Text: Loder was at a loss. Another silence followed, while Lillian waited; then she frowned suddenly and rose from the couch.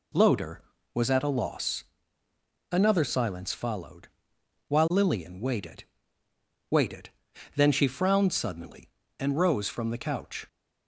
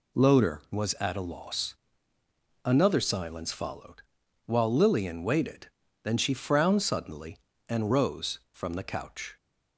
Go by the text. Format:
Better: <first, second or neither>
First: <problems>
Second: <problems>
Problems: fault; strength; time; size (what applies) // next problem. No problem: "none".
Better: second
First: says "waited" twice; at 6.7 s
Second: none